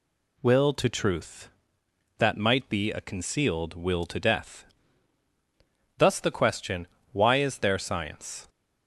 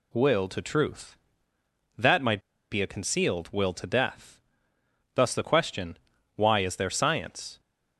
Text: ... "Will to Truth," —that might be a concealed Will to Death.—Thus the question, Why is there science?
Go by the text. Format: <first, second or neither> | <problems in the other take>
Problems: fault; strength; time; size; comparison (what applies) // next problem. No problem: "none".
first | pauses between "might" and "be"; slight; at 2.4 s; 0.30 s long